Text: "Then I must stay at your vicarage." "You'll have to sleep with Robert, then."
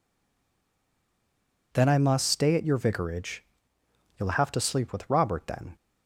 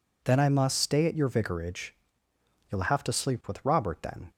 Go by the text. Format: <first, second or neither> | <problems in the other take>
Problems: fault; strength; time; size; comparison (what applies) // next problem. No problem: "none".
second | stays silent before the first word; noticeable; until 1.7 s; 1.7 s long